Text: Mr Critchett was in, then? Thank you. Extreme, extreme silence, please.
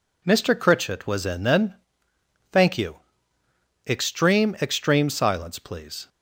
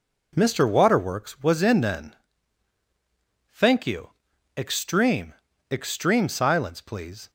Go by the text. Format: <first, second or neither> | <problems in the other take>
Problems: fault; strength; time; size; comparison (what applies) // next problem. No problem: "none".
first | says "Waterworks" for "Critchett"; at 0.6 s